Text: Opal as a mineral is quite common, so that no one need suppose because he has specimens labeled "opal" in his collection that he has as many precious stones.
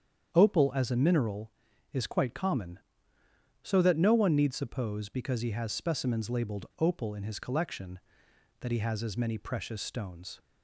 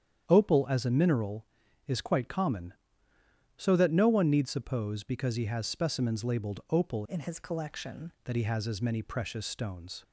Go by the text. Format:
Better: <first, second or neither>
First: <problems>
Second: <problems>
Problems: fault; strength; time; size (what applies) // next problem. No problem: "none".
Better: first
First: starts louder than the rest; strong; until 1.3 s; 8.5 dB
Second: starts louder than the rest; strong; until 1.3 s; 9 dB // changes voice from "in" to "collection"; from 7.0 to 8.1 s; 1.1 s long